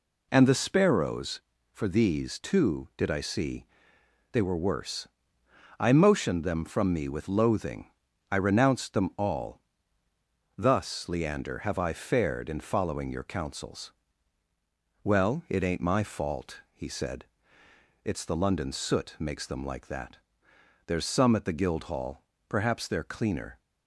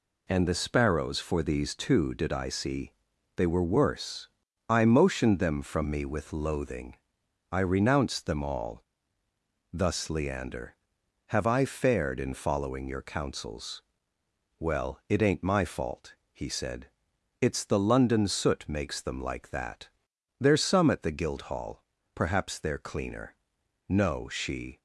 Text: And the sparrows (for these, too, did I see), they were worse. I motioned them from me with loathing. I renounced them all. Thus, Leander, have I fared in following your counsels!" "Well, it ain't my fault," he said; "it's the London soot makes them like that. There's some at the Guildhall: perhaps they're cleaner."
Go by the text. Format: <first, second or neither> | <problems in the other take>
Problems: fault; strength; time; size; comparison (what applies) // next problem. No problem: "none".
first | goes on to say "No she"; noticeable; from 23.8 s on; 0.92 s long